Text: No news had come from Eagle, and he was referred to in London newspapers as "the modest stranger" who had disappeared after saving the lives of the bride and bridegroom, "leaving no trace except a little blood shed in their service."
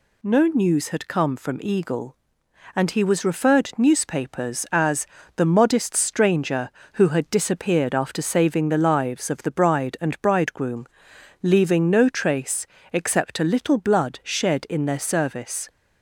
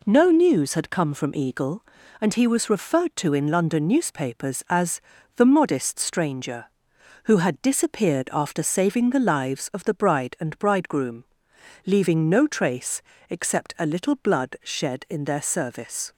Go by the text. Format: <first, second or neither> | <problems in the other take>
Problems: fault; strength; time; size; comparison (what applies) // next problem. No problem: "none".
second | skips "to in London"; at 3.7 s // pauses between "as" and "the"; slight; at 5.0 s; 0.30 s long; slight in the second // pauses between "trace" and "except"; slight; at 12.6 s; 0.26 s long; slight in the second